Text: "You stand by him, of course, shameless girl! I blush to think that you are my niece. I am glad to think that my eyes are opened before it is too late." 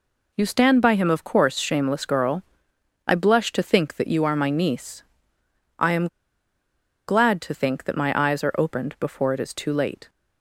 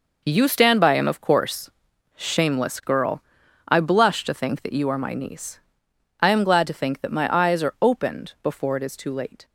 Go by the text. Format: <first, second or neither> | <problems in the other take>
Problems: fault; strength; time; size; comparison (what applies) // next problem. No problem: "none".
second | pauses between "am" and "glad"; at 6.0 s; 1.0 s long